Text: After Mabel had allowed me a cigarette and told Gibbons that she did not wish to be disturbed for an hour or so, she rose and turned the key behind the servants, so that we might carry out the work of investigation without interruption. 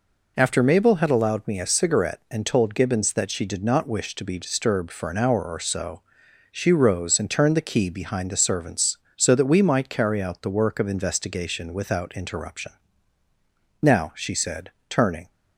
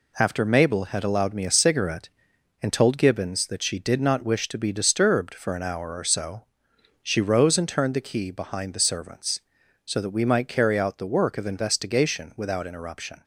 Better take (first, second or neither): second